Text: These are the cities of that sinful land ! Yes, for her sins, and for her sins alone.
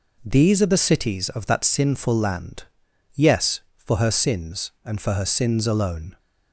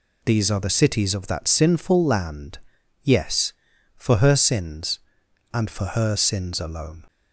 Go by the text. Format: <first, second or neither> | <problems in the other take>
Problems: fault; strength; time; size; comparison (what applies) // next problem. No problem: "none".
neither | none